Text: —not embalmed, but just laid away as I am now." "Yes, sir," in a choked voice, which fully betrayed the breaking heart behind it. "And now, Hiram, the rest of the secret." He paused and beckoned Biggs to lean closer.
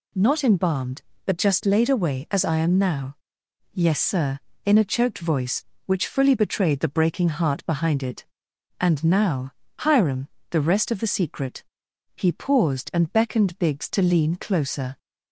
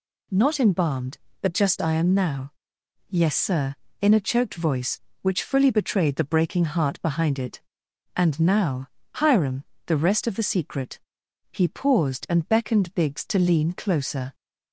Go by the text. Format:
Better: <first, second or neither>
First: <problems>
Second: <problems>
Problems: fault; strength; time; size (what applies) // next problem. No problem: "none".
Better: first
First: none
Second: skips "laid away as"; at 1.8 s